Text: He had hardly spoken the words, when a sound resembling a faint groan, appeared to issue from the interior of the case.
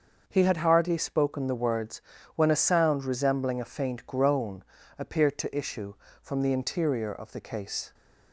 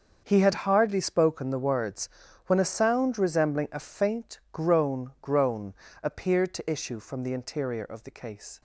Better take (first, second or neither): first